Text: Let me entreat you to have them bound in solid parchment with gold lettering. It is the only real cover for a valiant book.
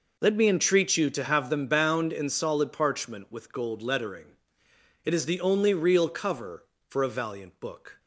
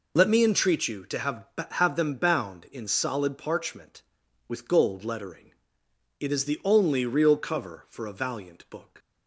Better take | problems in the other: first | says "have" twice; at 1.7 s

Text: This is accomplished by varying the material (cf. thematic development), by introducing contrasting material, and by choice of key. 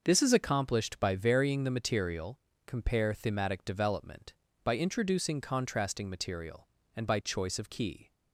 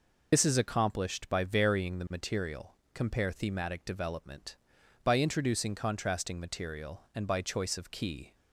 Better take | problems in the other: first | loses the start of "This"; at 0.3 s; 55 ms

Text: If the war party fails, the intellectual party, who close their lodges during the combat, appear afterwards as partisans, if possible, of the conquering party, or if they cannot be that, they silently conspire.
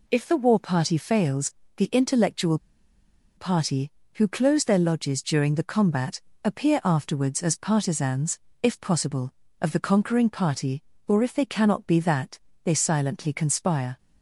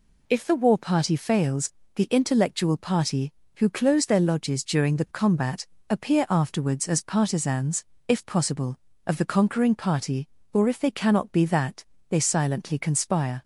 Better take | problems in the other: second | pauses between "intellectual" and "party"; noticeable; at 2.5 s; 0.78 s long

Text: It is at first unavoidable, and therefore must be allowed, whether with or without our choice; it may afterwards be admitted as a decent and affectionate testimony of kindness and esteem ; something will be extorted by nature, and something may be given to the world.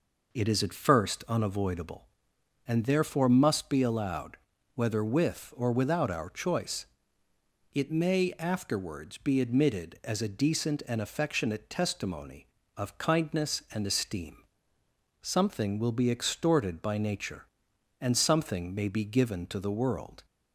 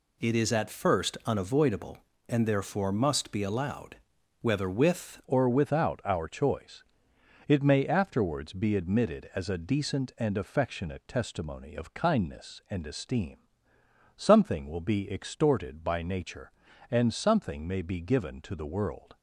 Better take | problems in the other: first | changes voice at "or"; from 5.2 s on; 13.9 s long

